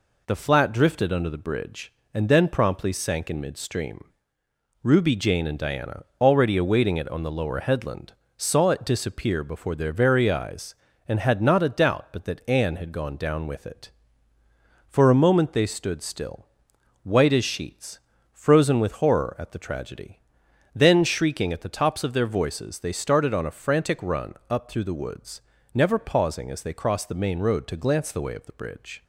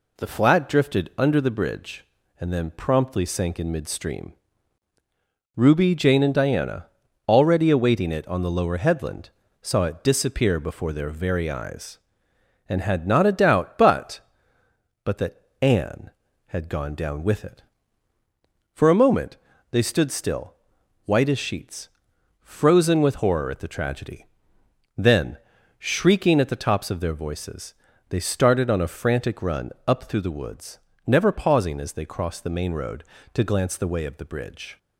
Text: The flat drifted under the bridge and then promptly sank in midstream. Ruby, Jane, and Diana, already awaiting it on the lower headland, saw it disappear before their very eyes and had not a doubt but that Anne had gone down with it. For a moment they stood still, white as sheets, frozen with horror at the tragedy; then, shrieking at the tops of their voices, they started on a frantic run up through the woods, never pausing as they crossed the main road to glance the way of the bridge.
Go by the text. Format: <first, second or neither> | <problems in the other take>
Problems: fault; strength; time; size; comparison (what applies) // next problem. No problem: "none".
first | says "but" twice; at 15.0 s // pauses between "that" and "Anne"; slight; at 15.3 s; 0.22 s long // pauses between "moment" and "they"; slight; at 19.3 s; 0.36 s long // pauses between "run" and "up"; slight; at 29.7 s; 0.16 s long